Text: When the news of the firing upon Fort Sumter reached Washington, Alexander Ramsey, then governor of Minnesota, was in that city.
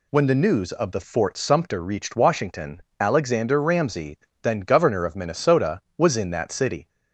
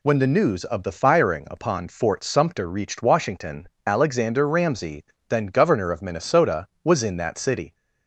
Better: second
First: skips "firing upon"; at 1.0 s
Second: none

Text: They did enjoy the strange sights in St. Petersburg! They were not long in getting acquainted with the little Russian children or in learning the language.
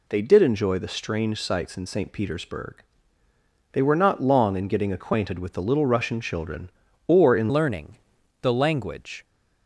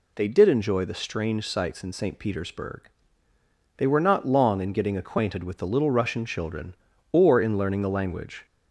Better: second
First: changes voice at "learning"; from 7.5 s on; 1.7 s long // pauses between "learning" and "the"; at 7.9 s; 0.44 s long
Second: none

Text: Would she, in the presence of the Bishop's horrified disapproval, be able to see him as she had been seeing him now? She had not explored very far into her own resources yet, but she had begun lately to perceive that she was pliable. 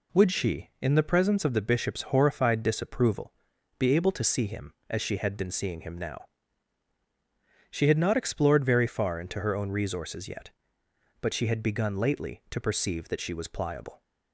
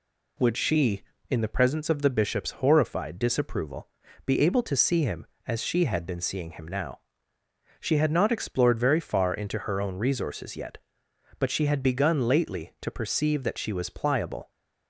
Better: neither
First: none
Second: none

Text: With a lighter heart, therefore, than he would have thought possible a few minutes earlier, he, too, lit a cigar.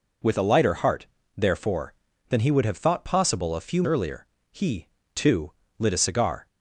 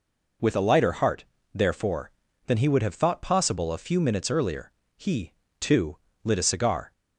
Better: second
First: skips "minutes"; at 3.8 s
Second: none

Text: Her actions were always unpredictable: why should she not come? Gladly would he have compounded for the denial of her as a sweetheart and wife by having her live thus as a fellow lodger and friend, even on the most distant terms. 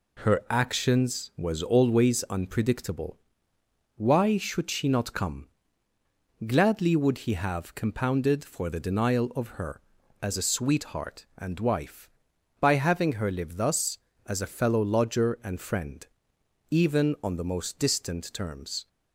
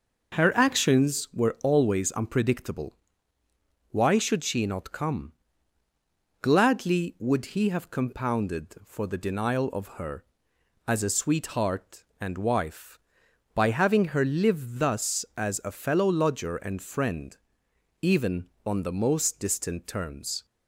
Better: second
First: says "was" for "were"; at 1.3 s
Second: none

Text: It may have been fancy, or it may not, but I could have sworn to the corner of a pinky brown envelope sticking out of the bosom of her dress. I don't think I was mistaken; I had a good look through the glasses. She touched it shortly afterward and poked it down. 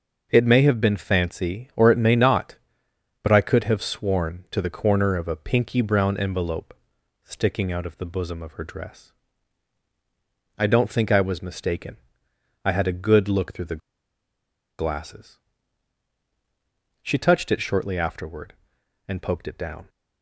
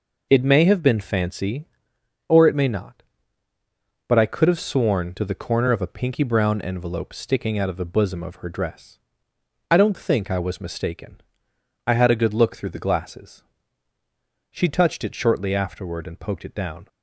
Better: second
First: starts louder than the rest; until 1.3 s; 6 dB // pauses between "envelope" and "sticking"; noticeable; at 6.7 s; 0.52 s long // pauses between "the" and "glasses"; at 13.8 s; 1.0 s long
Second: none

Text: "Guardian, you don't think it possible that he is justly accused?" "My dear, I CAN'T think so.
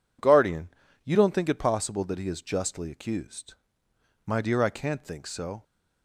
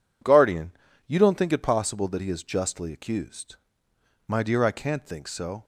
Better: neither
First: none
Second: none

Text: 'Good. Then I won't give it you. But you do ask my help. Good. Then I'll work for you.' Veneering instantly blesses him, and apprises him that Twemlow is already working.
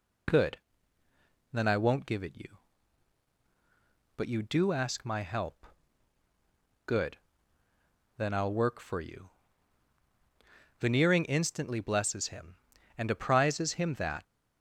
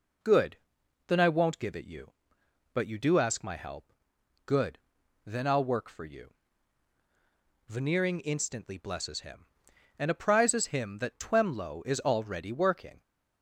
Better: second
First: stops before "Twemlow is already working"; at 14.2 s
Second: none

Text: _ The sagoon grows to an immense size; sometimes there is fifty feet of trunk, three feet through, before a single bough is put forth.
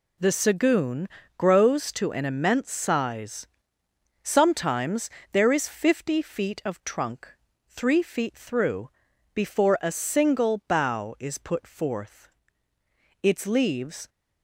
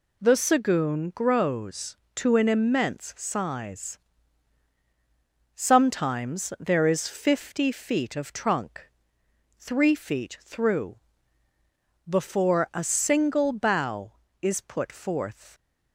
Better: second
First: pauses between "sagoon" and "grows"; slight; at 1.0 s; 0.30 s long // pauses between "sometimes" and "there"; slight; at 5.0 s; 0.22 s long // goes on to say "Its leaves"; noticeable; from 13.2 s on; 0.86 s long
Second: none

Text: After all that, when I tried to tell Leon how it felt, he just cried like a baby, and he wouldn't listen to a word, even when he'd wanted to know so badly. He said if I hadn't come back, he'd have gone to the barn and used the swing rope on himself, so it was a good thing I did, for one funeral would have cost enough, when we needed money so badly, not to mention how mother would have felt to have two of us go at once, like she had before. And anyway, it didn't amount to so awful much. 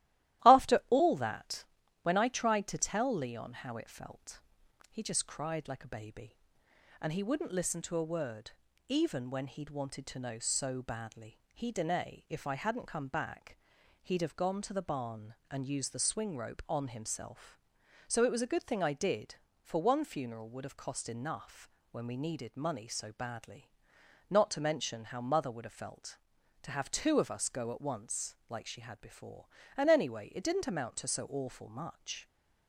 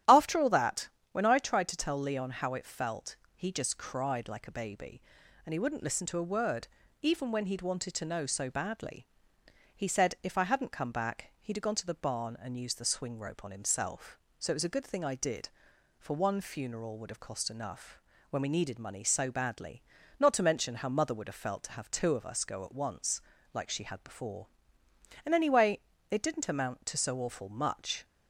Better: second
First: starts louder than the rest; strong; until 1.5 s; 15 dB // says "dene" for "said"; at 11.7 s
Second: starts louder than the rest; strong; until 1.3 s; 12 dB

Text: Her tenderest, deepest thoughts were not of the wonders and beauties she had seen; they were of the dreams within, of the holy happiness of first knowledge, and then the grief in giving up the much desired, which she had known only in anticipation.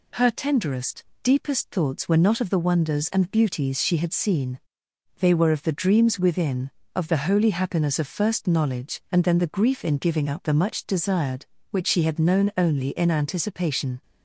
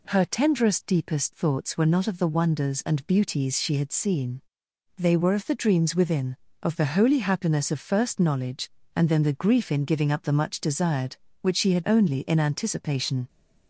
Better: first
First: none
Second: skips "known"; at 11.8 s

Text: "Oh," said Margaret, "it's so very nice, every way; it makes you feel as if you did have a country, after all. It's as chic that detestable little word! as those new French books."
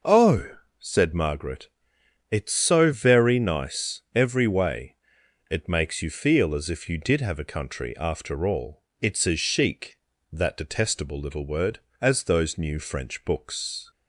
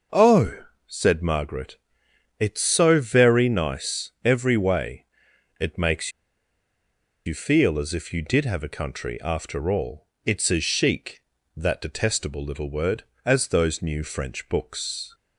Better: first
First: none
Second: pauses between "makes" and "you"; at 6.1 s; 1.1 s long

